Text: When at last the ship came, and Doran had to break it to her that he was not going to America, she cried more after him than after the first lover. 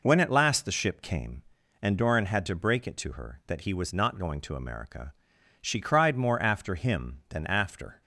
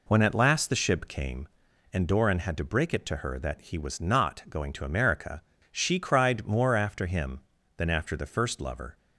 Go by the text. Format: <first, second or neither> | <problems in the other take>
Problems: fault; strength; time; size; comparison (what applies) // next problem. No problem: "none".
second | stops before "the first lover"; at 8.0 s